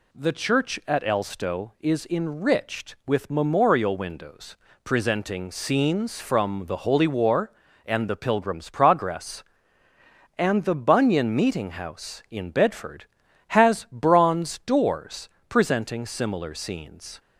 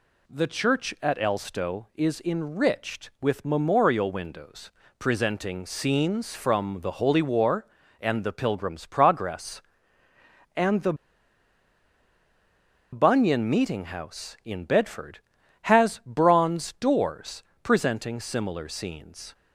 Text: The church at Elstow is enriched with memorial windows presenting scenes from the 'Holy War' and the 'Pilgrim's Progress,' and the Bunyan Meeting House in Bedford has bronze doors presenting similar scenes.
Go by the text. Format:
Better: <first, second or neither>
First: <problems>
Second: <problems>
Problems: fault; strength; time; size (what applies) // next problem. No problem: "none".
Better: first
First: pauses between "windows" and "presenting"; slight; at 4.5 s; 0.26 s long // pauses between "doors" and "presenting"; slight; at 15.2 s; 0.22 s long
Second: pauses between "windows" and "presenting"; slight; at 4.7 s; 0.26 s long // pauses between "the" and "Bunyan"; strong; at 10.9 s; 1.9 s long // pauses between "doors" and "presenting"; slight; at 17.4 s; 0.22 s long